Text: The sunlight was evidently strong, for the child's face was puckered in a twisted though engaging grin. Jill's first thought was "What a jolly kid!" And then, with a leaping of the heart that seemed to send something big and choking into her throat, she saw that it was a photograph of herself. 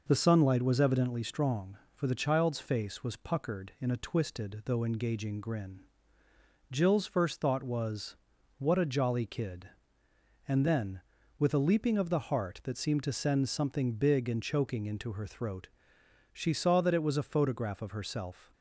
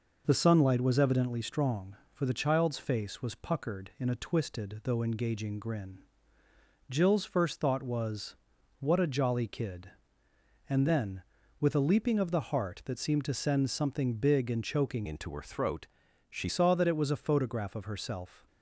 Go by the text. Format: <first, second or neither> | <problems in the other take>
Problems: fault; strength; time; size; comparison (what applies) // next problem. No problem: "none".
first | pauses between "was" and "What"; noticeable; at 8.3 s; 0.46 s long; also in the first // changes voice from "into" to "she"; from 15.0 to 16.4 s; 1.4 s long